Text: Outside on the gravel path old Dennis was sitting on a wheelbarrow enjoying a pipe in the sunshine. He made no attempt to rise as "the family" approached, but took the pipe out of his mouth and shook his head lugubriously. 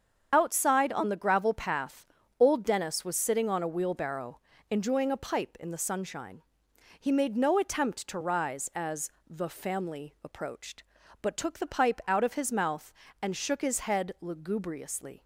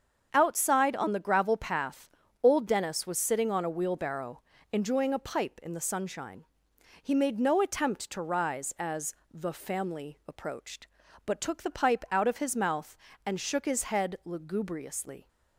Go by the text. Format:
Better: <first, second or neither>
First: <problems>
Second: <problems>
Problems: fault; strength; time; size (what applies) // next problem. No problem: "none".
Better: second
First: loses the start of "Outside"; at 0.3 s; 40 ms // starts louder than the rest; strong; until 1.3 s; 7 dB // pauses between "path" and "old"; slight; at 2.0 s; 0.34 s long // pauses between "wheelbarrow" and "enjoying"; slight; at 4.3 s; 0.30 s long // pauses between "as" and "the"; slight; at 9.0 s; 0.18 s long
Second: starts louder than the rest; until 1.3 s; 7 dB // pauses between "path" and "old"; slight; at 2.0 s; 0.34 s long // pauses between "wheelbarrow" and "enjoying"; slight; at 4.4 s; 0.30 s long // pauses between "as" and "the"; slight; at 9.1 s; 0.18 s long